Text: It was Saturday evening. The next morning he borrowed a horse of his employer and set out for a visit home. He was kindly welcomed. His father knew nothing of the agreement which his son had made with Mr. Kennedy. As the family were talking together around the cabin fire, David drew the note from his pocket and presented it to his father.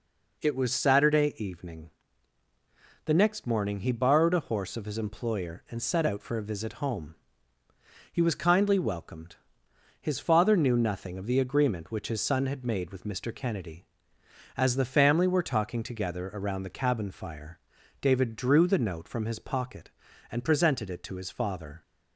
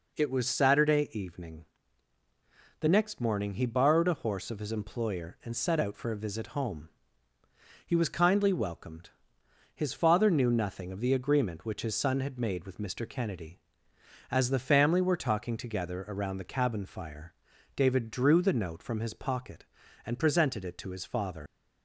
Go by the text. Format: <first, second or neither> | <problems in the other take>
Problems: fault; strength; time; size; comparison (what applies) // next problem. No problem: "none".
first | leaves "father" unfinished; at 21.4 s; 100 ms